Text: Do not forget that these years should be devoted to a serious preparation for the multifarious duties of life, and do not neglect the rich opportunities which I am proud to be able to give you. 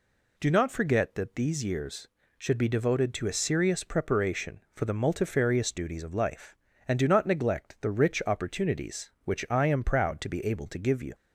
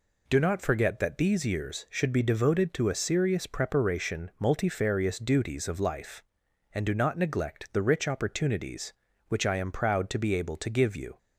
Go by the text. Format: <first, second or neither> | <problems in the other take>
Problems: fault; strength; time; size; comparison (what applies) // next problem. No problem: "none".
first | skips "for the"; at 4.3 s